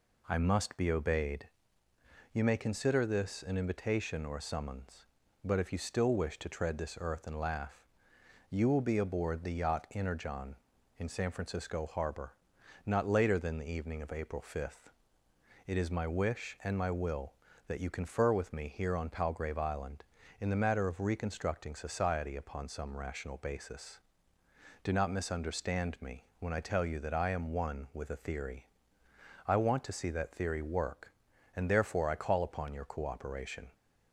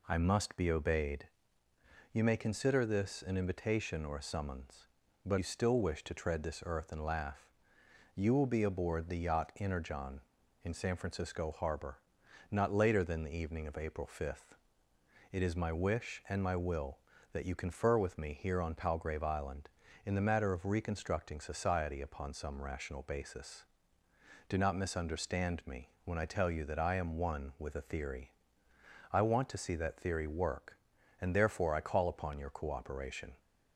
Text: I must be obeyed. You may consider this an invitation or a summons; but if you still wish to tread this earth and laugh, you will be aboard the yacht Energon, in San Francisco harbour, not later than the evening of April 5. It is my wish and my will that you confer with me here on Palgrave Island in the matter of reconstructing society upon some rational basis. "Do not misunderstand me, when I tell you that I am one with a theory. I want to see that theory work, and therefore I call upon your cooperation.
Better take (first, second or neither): first